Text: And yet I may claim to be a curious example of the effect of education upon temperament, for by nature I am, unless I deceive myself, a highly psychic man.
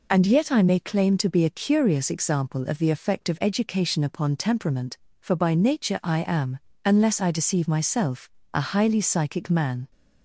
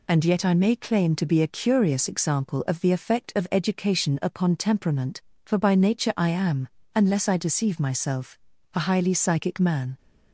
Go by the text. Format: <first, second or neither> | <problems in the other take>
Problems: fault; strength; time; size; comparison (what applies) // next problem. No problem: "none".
neither | none